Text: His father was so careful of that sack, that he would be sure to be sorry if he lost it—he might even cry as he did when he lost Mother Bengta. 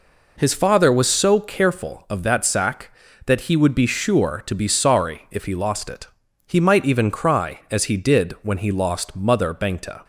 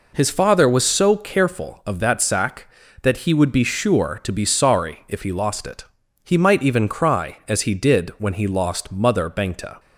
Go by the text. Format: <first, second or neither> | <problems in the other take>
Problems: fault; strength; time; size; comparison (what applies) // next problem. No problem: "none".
neither | none